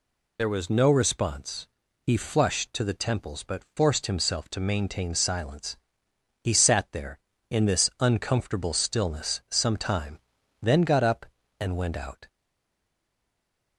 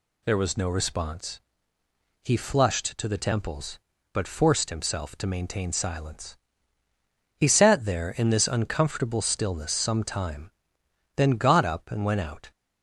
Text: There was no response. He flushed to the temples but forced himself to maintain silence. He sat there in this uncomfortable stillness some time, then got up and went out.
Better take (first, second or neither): second